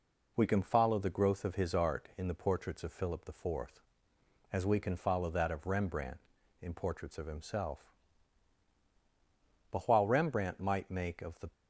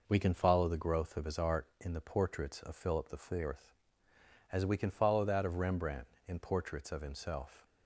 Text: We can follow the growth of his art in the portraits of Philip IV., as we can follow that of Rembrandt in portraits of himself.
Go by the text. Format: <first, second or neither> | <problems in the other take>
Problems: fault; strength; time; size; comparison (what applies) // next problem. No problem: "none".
second | goes on to say "But while Rembrandt might make of the"; strong; from 9.7 s on; 1.8 s long